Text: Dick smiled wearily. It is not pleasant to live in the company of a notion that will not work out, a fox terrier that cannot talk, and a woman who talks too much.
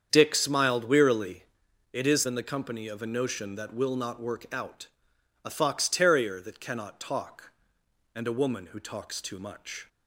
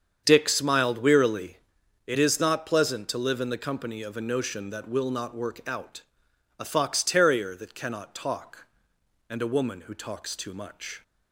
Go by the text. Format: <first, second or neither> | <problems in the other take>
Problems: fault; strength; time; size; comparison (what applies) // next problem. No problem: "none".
second | starts louder than the rest; strong; until 1.1 s; 8 dB; strong in the second // skips "not pleasant to live"; at 2.2 s